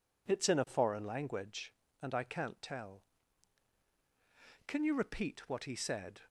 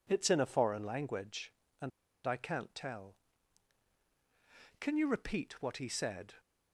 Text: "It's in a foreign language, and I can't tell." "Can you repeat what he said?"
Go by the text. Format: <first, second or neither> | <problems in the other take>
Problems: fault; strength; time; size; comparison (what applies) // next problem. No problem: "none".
first | pauses between "and" and "I"; slight; at 1.9 s; 0.35 s long